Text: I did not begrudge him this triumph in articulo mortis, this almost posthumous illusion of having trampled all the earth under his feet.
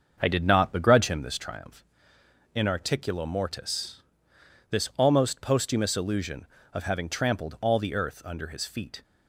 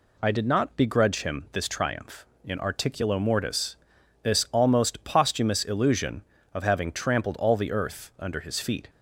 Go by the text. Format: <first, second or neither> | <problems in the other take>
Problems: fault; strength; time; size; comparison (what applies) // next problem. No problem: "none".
second | starts louder than the rest; until 1.4 s; 7 dB